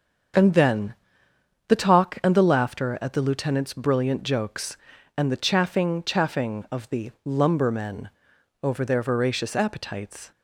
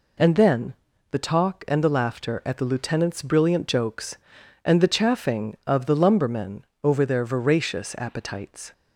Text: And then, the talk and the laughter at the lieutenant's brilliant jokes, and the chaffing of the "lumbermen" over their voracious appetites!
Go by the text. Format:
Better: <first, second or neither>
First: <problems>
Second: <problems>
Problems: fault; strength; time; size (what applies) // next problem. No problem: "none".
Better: second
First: starts louder than the rest; until 2.0 s; 7 dB // says "chaffing" twice; at 6.0 s // pauses between "lumbermen" and "over"; noticeable; at 8.0 s; 0.52 s long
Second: pauses between "lumbermen" and "over"; slight; at 6.6 s; 0.18 s long